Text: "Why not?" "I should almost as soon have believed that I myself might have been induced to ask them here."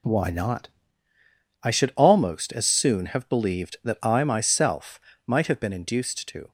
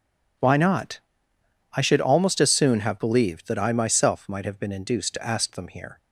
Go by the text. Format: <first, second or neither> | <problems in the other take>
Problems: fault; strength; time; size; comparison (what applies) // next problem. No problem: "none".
second | pauses between "myself" and "might"; slight; at 5.0 s; 0.24 s long // stops before "ask them here"; at 6.4 s